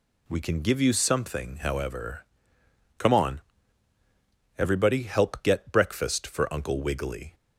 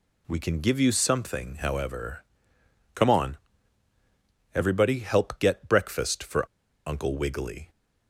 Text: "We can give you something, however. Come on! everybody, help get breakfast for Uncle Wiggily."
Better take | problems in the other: first | pauses between "for" and "Uncle"; at 6.4 s; 0.40 s long

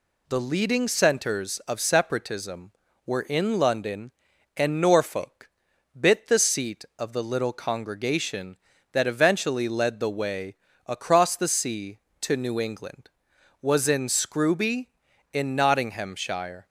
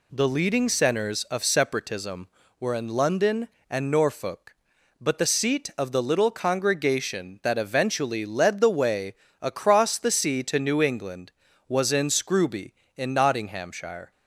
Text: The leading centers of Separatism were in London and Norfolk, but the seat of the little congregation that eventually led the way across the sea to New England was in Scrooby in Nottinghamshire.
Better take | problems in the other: second | says "bit" for "but"; at 5.9 s // pauses between "way" and "across"; slight; at 10.5 s; 0.32 s long; slight in the second

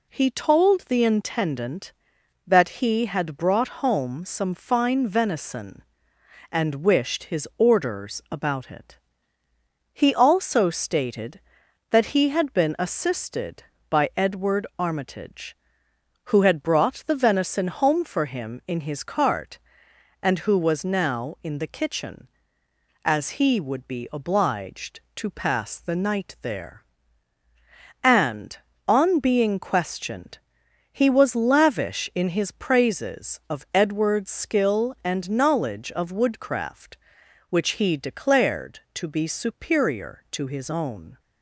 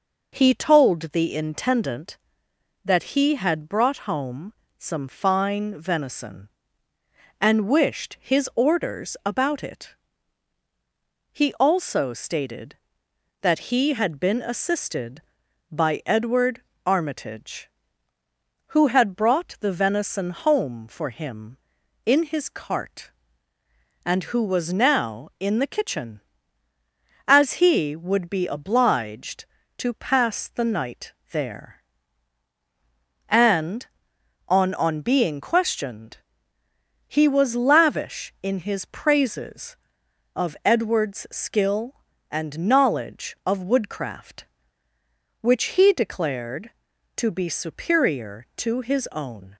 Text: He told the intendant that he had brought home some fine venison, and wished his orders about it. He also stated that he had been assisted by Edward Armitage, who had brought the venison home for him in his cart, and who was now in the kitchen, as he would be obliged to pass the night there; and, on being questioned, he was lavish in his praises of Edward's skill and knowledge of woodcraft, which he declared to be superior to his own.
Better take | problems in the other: first | pauses between "home" and "some"; slight; at 4.5 s; 0.28 s long // pauses between "Edward" and "Armitage"; slight; at 16.6 s; 0.22 s long // pauses between "night" and "there"; slight; at 31.1 s; 0.18 s long // says "on" twice; at 34.7 s

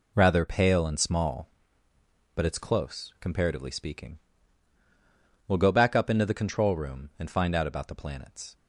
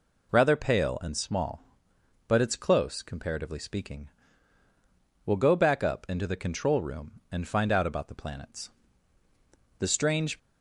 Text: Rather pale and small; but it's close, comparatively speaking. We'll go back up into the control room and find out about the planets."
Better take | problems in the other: first | goes on to say "The strange"; from 9.7 s on; 0.60 s long

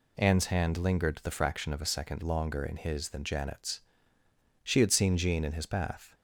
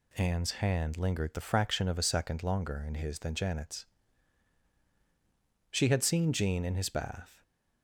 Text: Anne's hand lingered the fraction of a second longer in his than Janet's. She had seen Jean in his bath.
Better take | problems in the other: neither | none

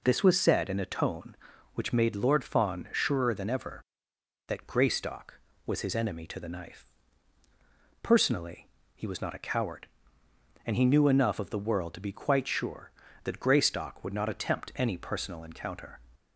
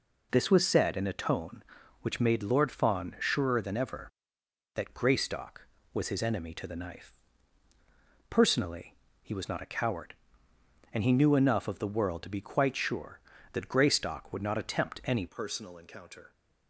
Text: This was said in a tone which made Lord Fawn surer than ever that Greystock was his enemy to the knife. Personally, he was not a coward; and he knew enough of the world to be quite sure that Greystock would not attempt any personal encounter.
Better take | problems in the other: first | changes voice at "personal"; from 15.2 s on; 1.1 s long

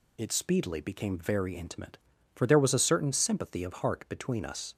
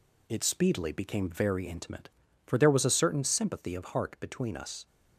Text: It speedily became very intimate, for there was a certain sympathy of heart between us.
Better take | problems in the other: first | gets quieter; slight; throughout; 2.5 dB

